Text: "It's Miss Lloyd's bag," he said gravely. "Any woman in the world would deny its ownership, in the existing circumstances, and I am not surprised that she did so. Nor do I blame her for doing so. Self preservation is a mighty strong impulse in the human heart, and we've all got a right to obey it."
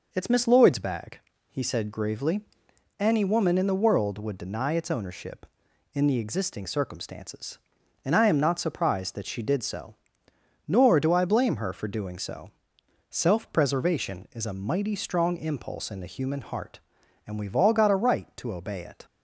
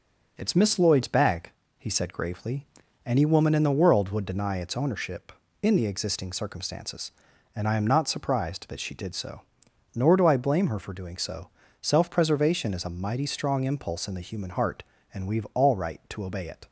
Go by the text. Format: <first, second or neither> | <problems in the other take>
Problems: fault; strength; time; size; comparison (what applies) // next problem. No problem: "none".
first | skips "got a"; at 15.7 s